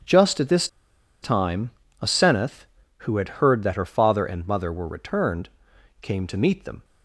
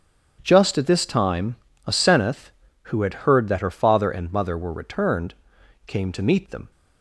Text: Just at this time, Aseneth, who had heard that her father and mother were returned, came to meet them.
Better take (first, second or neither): second